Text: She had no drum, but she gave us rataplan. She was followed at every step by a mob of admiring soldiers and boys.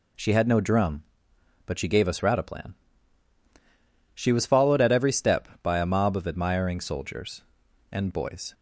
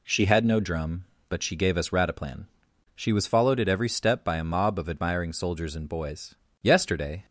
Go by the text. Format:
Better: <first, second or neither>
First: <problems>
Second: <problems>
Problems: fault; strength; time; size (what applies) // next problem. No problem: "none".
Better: first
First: none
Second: goes on to say "Yesterday"; noticeable; from 6.6 s on; 0.64 s long